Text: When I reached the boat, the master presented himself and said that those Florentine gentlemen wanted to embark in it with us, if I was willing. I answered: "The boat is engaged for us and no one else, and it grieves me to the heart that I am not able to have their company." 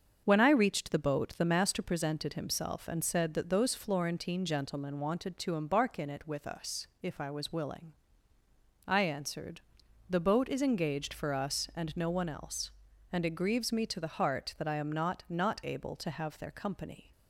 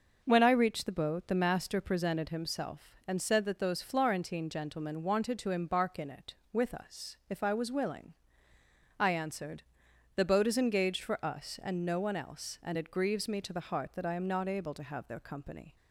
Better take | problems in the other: second | starts louder than the rest; until 1.2 s; 7 dB; also in the second // says "not" twice; at 15.2 s

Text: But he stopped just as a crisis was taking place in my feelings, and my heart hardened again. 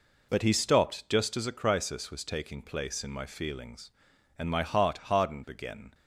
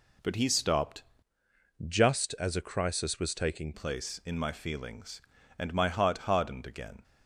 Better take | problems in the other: first | changes voice from "just" to "taking"; from 1.8 to 3.7 s; 1.9 s long

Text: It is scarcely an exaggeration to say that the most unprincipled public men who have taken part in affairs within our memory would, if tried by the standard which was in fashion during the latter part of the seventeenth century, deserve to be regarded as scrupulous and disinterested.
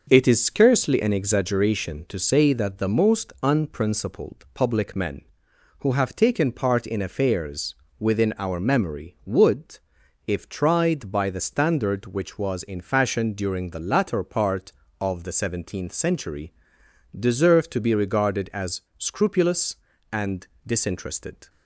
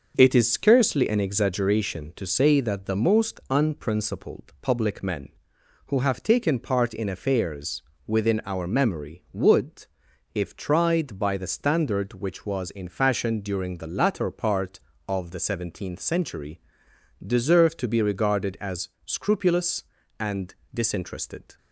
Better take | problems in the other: neither | starts louder than the rest; the same in both // pauses between "affairs" and "within"; slight; the same in both // pauses between "as" and "scrupulous"; slight; the same in both // pauses between "and" and "disinterested"; slight; the same in both

